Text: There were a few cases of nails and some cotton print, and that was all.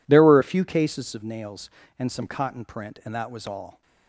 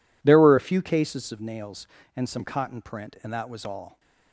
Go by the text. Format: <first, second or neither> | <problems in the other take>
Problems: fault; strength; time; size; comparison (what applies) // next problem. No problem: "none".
neither | none